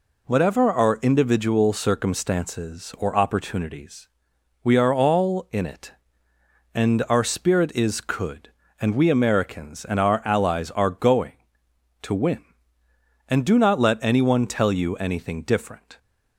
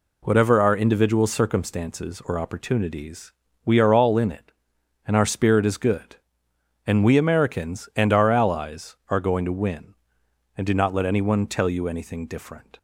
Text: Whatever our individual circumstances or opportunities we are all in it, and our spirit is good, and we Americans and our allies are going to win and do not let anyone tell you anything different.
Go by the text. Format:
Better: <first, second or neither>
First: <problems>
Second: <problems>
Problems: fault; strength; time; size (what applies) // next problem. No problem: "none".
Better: second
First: pauses between "opportunities" and "we"; noticeable; at 4.0 s; 0.54 s long // says "could" for "good"; at 8.0 s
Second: pauses between "opportunities" and "we"; slight; at 3.3 s; 0.32 s long